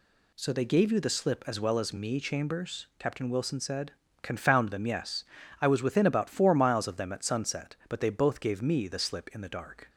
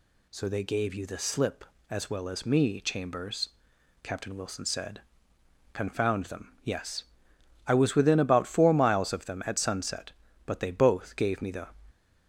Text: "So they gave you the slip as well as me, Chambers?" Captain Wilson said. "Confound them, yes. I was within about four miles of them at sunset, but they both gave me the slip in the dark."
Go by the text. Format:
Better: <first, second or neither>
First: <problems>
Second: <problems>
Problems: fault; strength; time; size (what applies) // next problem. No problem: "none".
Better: first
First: none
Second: stops before "slip in the dark"; at 11.9 s